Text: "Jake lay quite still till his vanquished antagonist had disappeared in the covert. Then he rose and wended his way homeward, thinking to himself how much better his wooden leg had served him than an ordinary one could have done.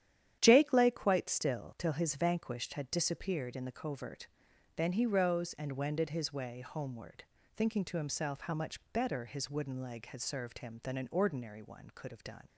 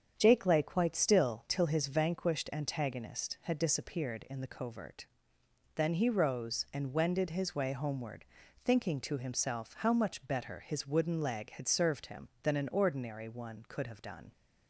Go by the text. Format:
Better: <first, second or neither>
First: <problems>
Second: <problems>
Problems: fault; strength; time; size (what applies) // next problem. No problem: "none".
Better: second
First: starts louder than the rest; strong; until 1.4 s; 10.5 dB // skips "antagonist"; at 2.7 s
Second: starts louder than the rest; strong; until 1.1 s; 7.5 dB